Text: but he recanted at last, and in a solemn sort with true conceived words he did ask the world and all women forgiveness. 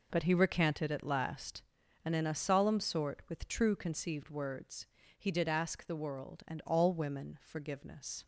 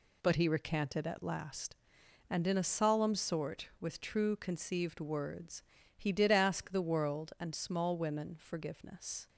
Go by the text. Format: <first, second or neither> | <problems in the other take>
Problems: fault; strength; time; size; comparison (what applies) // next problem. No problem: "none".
first | pauses between "words" and "he"; slight; at 5.6 s; 0.34 s long; slight in the first // says "small" for "all"; at 7.5 s